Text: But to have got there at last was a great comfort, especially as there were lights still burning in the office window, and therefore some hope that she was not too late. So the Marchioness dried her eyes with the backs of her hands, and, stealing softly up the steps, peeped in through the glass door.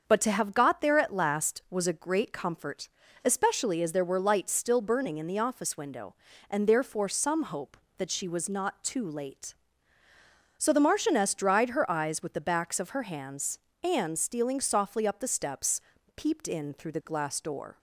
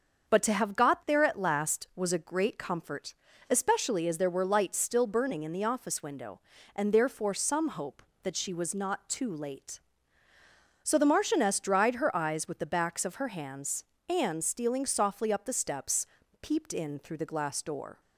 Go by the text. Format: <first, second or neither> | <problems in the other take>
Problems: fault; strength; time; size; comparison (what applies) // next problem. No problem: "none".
neither | starts louder than the rest; the same in both